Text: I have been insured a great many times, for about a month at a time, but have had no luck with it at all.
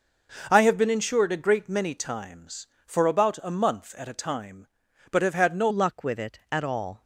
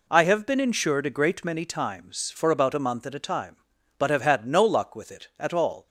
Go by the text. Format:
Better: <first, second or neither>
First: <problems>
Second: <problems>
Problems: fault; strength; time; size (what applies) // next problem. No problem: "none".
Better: second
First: changes voice at "luck"; from 5.6 s on; 1.4 s long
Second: none